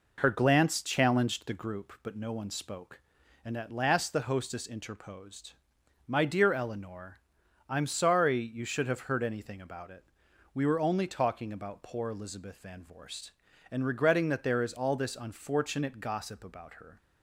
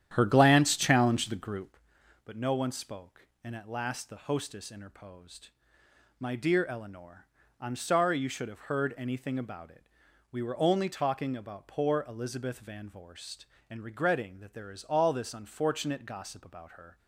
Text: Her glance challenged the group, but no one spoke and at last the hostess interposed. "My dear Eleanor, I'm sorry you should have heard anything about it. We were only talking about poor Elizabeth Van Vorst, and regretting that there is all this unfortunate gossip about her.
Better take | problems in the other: first | starts louder than the rest; strong; until 1.8 s; 10.5 dB

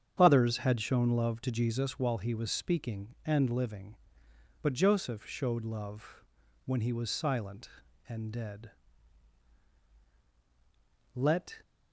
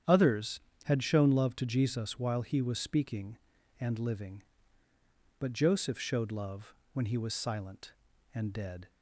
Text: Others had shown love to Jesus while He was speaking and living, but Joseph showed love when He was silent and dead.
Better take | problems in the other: second | starts louder than the rest; strong; until 1.1 s; 8 dB; strong in the second // pauses between "love" and "when"; at 6.2 s; 0.42 s long; slight in the second // goes on to say "Let"; slight; from 11.1 s on; 0.44 s long

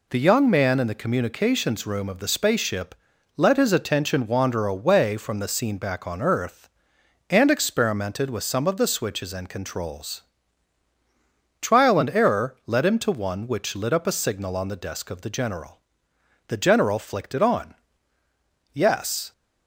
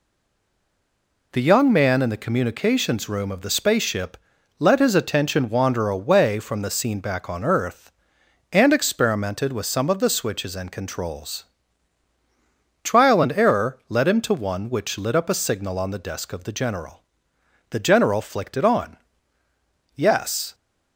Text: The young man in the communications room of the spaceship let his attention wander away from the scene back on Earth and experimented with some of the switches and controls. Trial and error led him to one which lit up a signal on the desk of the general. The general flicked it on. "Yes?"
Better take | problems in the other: first | stays silent before the first word; noticeable; until 1.3 s; 1.3 s long // pauses between "spaceship" and "let"; at 4.1 s; 0.42 s long; also in the first

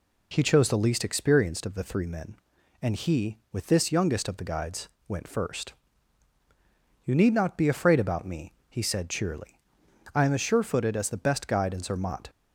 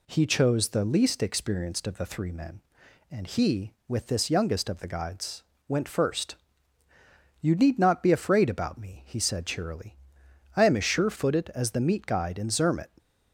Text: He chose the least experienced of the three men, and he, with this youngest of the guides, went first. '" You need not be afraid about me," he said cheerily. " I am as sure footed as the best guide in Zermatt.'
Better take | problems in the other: first | says "meat" for "best"; at 11.7 s

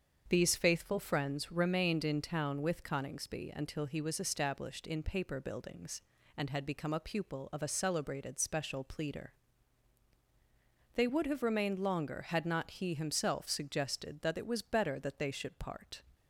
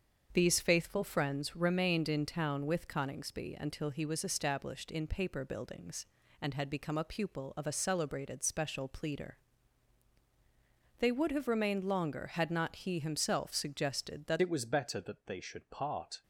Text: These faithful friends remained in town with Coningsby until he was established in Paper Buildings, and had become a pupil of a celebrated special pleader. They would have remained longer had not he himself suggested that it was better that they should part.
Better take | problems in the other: first | starts louder than the rest; until 1.3 s; 7 dB; also in the first // changes voice at "it"; from 14.4 s on; 1.8 s long

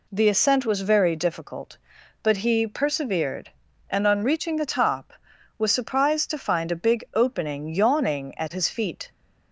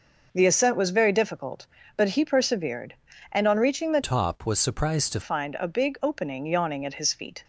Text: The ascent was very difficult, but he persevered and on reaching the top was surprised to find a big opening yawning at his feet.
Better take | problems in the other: first | starts louder than the rest; noticeable; until 1.3 s; 6 dB // changes voice from "top" to "to"; from 4.0 to 5.2 s; 1.2 s long

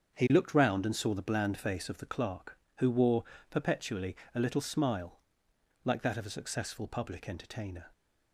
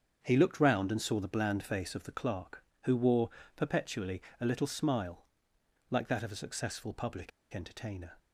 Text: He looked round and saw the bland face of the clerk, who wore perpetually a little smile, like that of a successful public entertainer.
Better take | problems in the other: first | starts louder than the rest; until 1.2 s; 7 dB; also in the first // pauses between "wore" and "perpetually"; slight; at 3.2 s; 0.26 s long; slight in the first // pauses between "perpetually" and "a"; slight; at 4.2 s; 0.18 s long; slight in the first // pauses between "public" and "entertainer"; slight; at 7.3 s; 0.23 s long

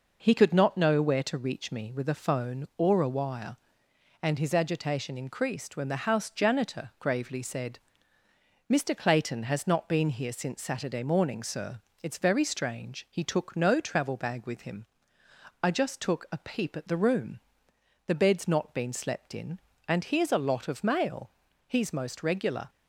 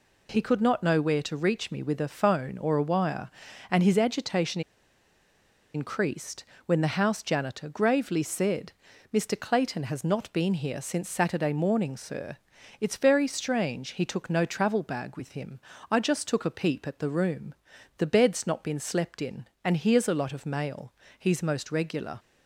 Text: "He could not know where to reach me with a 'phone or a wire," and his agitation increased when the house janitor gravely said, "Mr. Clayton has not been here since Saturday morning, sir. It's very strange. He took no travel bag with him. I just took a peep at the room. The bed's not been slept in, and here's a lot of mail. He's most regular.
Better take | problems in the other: first | pauses between "agitation" and "increased"; at 4.6 s; 1.1 s long // pauses between "increased" and "when"; slight; at 6.4 s; 0.24 s long

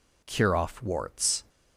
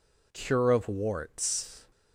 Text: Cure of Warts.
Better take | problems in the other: second | says "off" for "of"; at 0.5 s

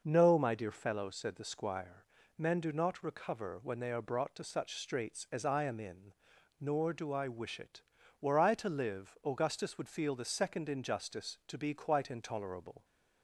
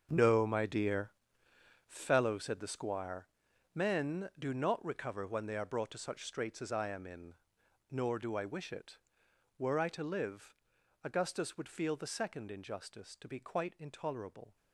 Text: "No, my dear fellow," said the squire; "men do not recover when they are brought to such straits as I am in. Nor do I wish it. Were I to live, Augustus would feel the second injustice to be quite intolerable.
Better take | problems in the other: first | gets quieter; strong; throughout; 12.5 dB // pauses between "dear" and "fellow"; noticeable; at 1.1 s; 0.74 s long

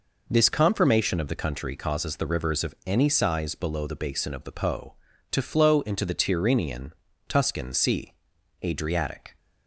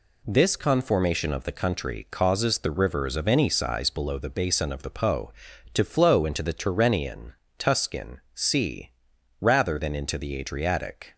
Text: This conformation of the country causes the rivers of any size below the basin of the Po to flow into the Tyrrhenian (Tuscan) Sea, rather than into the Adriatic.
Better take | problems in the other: second | skips "rather than into the"; at 8.3 s

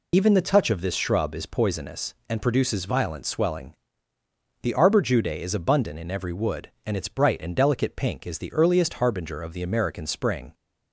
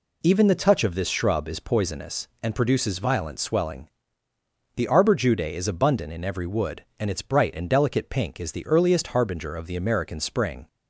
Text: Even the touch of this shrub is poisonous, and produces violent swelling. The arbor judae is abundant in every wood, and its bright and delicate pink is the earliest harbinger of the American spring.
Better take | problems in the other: second | loses the start of "Even"; at 0.1 s; 40 ms

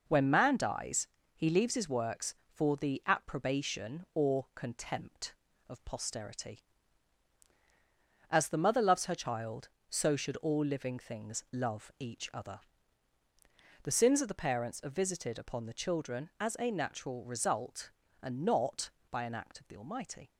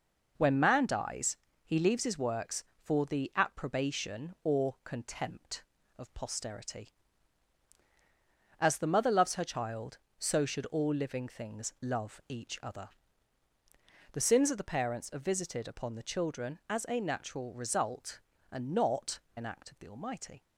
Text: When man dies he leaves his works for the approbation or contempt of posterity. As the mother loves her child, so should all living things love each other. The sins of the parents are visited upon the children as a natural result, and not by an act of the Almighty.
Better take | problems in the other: first | pauses between "dies" and "he"; slight; at 1.3 s; 0.28 s long; slight in the first // skips "by"; at 19.2 s

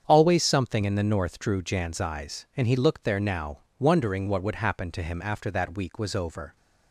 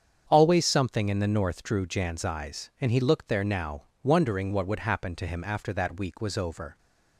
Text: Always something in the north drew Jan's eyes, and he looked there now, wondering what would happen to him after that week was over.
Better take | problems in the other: neither | starts louder than the rest; strong; the same in both

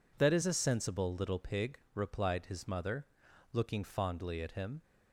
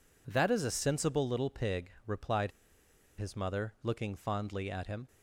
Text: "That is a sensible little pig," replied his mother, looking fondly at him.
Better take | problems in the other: first | pauses between "replied" and "his"; noticeable; at 2.4 s; 0.68 s long

